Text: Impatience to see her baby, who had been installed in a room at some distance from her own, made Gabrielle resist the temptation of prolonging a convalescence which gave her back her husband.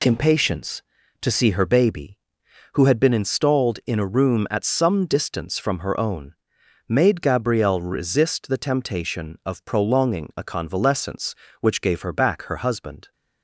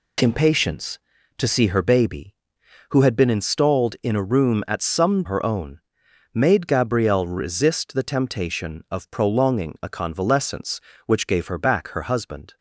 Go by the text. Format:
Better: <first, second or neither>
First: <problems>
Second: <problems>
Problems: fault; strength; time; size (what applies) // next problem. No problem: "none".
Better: first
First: none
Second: skips "distance from"; at 5.2 s